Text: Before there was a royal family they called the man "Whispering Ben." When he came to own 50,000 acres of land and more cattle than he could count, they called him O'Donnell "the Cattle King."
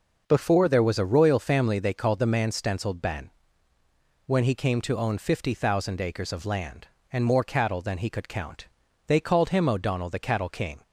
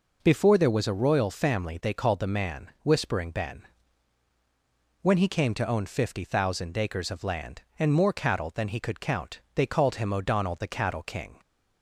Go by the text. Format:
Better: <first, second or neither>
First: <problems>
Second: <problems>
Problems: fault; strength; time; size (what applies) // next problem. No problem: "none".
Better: second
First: says "Stenciled" for "Whispering"; at 2.5 s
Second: none